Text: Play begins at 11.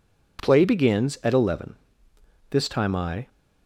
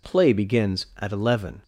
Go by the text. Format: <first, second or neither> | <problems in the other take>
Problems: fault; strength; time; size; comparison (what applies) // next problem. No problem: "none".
second | goes on to say "This time I"; noticeable; from 2.5 s on; 0.78 s long